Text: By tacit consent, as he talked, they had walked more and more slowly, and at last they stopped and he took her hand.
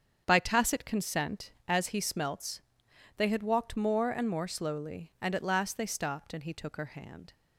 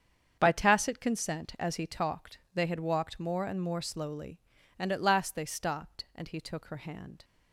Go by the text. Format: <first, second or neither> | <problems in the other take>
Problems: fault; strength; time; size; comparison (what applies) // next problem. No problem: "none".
second | starts louder than the rest; strong; until 1.2 s; 7.5 dB; strong in the second // says "smelts" for "talked"; at 2.0 s